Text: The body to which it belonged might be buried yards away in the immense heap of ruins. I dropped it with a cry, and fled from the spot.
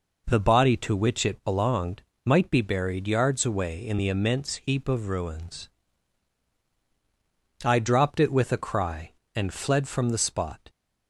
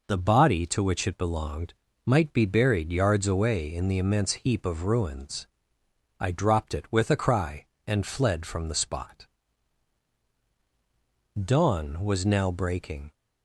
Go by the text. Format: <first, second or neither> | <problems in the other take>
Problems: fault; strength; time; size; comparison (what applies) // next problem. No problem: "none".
first | pauses between "belonged" and "might"; slight; at 1.7 s; 0.32 s long; slight in the first // goes on to say "Dawn was now breaking"; strong; from 11.4 s on; 1.6 s long